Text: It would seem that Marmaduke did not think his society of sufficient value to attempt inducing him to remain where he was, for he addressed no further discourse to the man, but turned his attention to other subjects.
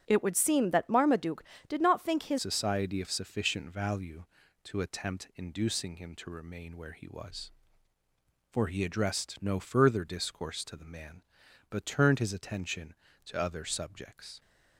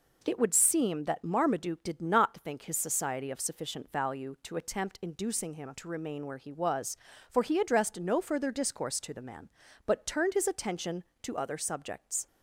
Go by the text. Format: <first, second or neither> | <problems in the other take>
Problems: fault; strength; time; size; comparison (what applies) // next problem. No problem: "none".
second | starts louder than the rest; strong; until 1.0 s; 8 dB // changes voice at "society"; from 2.3 s on; 12.0 s long